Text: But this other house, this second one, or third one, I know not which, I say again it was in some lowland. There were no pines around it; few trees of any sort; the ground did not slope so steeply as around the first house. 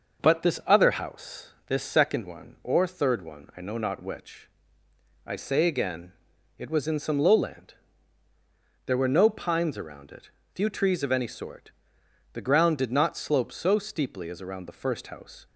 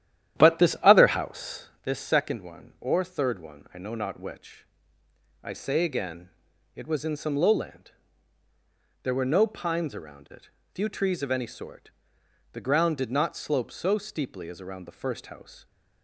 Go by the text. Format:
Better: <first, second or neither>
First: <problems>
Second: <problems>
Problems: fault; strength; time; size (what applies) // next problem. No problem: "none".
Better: first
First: pauses between "again" and "it"; noticeable; at 6.1 s; 0.46 s long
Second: starts louder than the rest; strong; until 1.8 s; 11 dB // pauses between "again" and "it"; noticeable; at 6.2 s; 0.46 s long